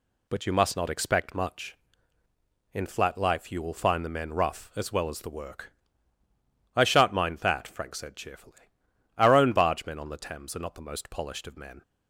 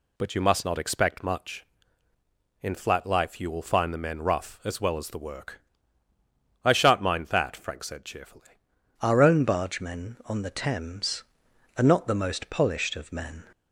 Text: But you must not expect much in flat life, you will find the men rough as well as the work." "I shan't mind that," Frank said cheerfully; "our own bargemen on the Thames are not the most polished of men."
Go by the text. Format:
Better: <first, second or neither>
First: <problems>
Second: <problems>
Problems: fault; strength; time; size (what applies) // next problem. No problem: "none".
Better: first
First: none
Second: changes voice at "our"; from 9.0 s on; 4.4 s long